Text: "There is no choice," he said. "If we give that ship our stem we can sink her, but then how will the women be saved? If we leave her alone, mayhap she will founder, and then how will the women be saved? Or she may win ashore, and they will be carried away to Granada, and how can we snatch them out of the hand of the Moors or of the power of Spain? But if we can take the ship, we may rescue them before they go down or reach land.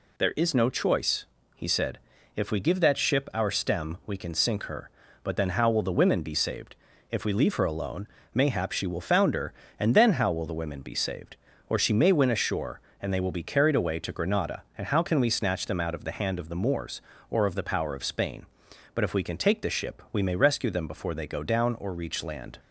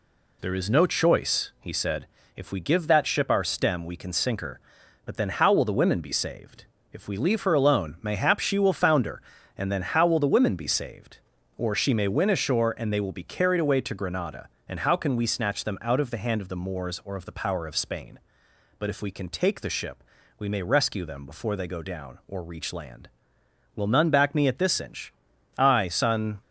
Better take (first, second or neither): first